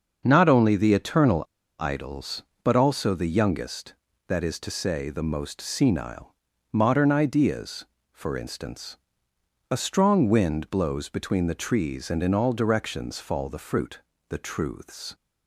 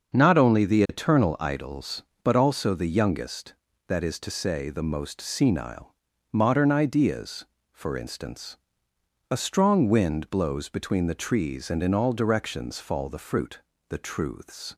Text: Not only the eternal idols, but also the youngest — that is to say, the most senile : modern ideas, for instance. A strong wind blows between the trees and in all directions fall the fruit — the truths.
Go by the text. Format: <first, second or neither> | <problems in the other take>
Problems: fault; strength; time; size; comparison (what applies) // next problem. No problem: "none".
second | starts louder than the rest; until 1.2 s; 6.5 dB; also in the second // pauses between "eternal" and "idols"; slight; at 1.4 s; 0.34 s long